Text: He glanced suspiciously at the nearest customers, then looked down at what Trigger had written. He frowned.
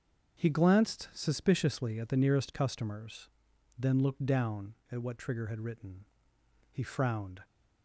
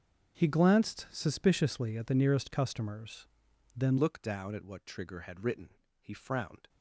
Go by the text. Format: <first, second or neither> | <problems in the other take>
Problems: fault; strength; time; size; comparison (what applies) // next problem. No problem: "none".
first | starts louder than the rest; until 1.4 s; 6.5 dB; also in the first // changes voice at "looked"; from 3.9 s on; 2.7 s long